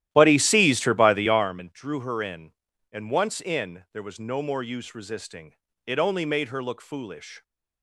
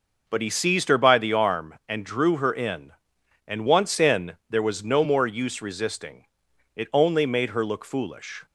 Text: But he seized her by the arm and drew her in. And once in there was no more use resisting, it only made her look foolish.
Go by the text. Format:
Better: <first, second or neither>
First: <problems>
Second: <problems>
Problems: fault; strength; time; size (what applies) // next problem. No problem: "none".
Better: second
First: starts louder than the rest; strong; until 1.6 s; 13 dB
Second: none